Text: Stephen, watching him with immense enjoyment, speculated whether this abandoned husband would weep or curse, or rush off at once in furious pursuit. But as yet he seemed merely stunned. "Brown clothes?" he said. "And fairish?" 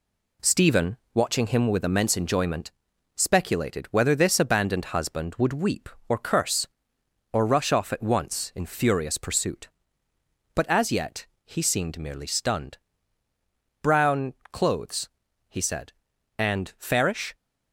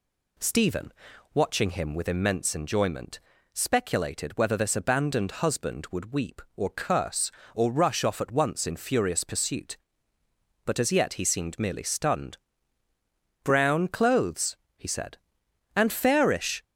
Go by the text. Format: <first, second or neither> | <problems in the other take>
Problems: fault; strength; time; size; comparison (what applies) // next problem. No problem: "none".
second | gets quieter; noticeable; throughout; 4.5 dB // pauses between "yet" and "he"; slight; at 11.2 s; 0.18 s long // pauses between "Brown" and "clothes"; slight; at 14.3 s; 0.18 s long